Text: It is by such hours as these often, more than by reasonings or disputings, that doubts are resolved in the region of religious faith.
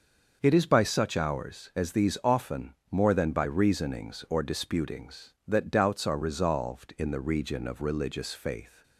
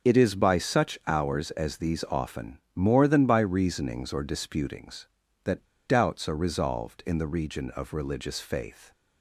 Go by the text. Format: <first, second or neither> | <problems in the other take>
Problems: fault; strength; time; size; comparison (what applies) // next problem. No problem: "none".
first | starts louder than the rest; strong; until 1.1 s; 7.5 dB; also in the first // pauses between "that" and "doubts"; slight; at 5.6 s; 0.21 s long